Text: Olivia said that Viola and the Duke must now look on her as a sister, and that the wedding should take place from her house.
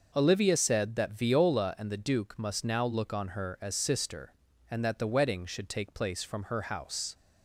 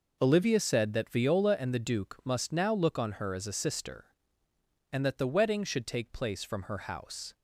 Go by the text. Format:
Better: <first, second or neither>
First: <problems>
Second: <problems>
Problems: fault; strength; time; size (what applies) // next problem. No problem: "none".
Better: second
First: skips "a"; at 3.7 s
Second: none